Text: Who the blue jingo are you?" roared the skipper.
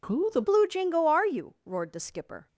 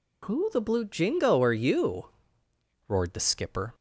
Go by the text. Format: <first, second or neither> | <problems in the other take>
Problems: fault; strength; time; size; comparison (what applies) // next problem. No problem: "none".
second | changes voice at "blue"; from 0.4 s on; 2.0 s long